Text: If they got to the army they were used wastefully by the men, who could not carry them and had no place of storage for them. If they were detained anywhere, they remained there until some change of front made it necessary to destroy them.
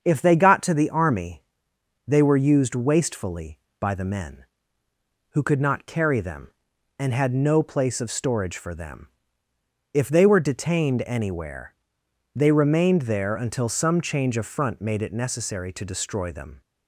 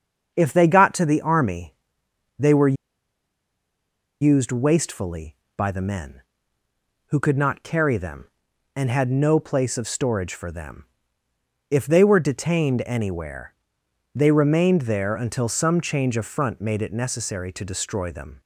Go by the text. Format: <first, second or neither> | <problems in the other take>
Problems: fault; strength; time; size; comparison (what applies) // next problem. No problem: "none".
first | starts louder than the rest; until 1.3 s; 7 dB; also in the first // pauses between "army" and "they"; noticeable; at 1.7 s; 0.64 s long; noticeable in the first // pauses between "were" and "used"; strong; at 2.7 s; 1.4 s long